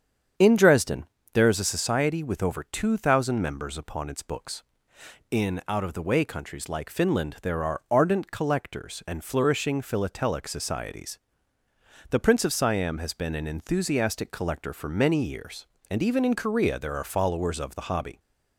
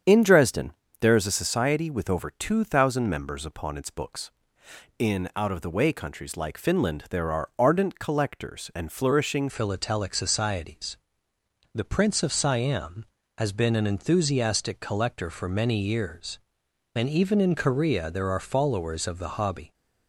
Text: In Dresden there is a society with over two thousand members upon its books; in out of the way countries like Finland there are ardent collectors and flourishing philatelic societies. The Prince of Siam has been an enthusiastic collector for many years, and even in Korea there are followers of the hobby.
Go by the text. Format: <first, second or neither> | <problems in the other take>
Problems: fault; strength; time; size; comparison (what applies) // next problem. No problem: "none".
first | starts louder than the rest; strong; until 1.3 s; 8 dB; strong in the first // pauses between "Dresden" and "there"; slight; at 0.7 s; 0.26 s long; slight in the first // changes voice at "philatelic"; from 9.4 s on; 10.3 s long